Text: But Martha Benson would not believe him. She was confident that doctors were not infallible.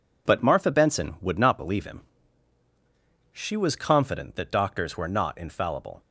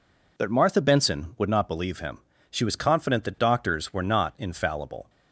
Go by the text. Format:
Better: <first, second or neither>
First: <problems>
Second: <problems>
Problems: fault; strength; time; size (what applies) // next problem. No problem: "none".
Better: neither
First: none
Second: none